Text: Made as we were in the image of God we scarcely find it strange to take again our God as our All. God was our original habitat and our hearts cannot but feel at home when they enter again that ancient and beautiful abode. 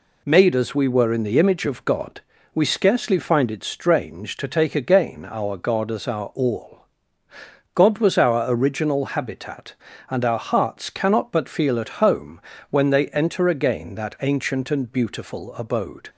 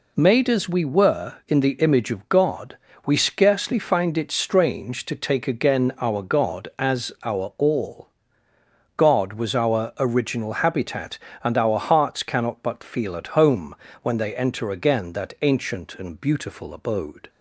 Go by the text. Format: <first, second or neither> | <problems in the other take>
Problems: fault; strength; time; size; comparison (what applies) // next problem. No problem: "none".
neither | pauses between "God" and "we"; slight; the same in both // pauses between "home" and "when"; slight; the same in both